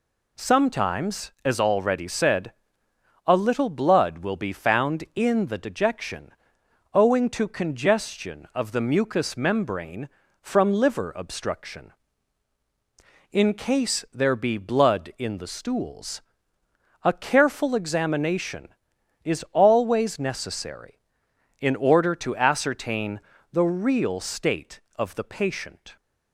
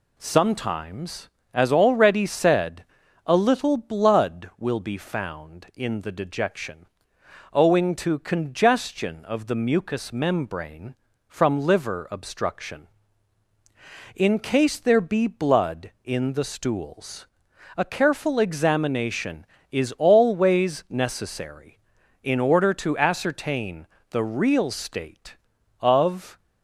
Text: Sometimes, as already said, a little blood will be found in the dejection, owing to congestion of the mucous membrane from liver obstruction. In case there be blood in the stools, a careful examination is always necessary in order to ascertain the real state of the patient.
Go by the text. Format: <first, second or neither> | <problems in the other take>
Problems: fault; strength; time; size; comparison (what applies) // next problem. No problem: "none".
first | pauses between "ascertain" and "the"; slight; at 23.8 s; 0.26 s long; slight in the first // stops before "the patient"; at 26.3 s